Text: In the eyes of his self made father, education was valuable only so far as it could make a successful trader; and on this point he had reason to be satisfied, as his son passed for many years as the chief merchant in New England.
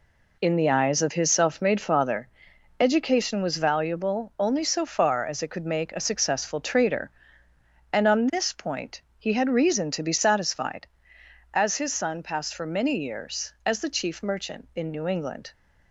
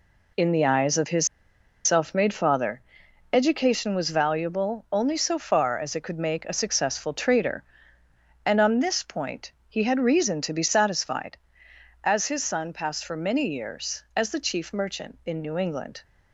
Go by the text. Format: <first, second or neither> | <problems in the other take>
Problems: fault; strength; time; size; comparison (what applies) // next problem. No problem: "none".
first | pauses between "his" and "self"; noticeable; at 1.2 s; 0.57 s long // pauses between "point" and "he"; slight; at 9.5 s; 0.16 s long; slight in the first